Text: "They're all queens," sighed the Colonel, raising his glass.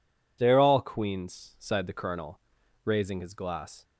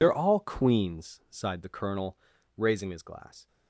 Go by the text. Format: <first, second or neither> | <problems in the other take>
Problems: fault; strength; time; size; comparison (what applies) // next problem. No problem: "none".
first | loses the start of "They're"; at 0.0 s; 45 ms